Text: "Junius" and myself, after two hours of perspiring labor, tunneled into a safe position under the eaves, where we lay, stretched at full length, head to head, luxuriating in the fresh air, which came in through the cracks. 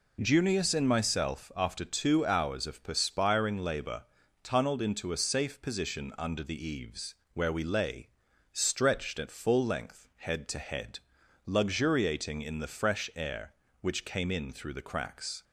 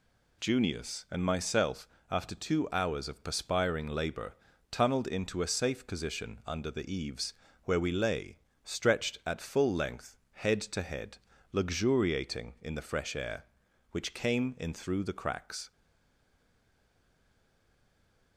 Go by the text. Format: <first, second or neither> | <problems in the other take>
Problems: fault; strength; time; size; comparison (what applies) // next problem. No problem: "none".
first | stays silent after the last word; strong; from 15.7 s on; 2.6 s long